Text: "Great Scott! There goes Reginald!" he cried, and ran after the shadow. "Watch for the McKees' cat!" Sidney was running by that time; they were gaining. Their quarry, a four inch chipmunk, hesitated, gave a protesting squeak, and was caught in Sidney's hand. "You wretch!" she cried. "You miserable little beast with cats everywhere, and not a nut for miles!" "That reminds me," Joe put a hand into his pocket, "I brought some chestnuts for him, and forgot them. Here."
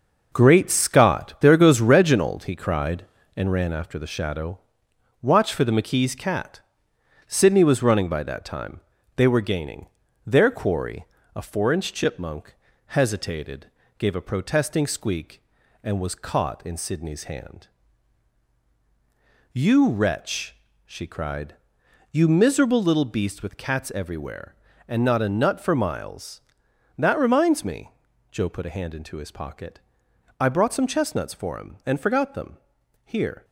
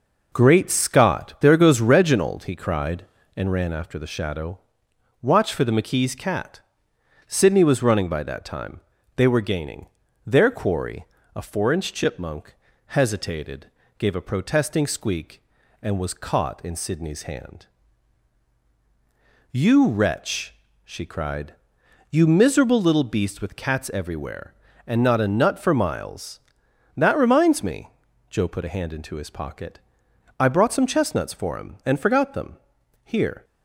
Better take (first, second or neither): second